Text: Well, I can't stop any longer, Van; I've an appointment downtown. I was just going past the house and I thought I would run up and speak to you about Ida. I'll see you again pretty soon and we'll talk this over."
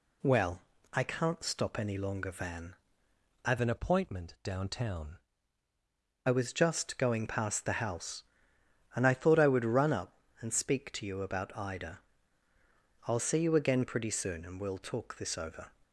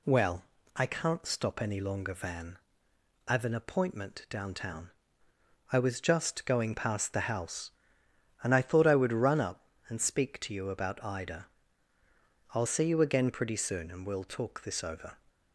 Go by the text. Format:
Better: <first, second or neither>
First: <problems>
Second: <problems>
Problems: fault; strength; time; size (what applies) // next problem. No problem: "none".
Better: second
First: changes voice from "an" to "I"; from 3.5 to 6.2 s; 2.7 s long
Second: none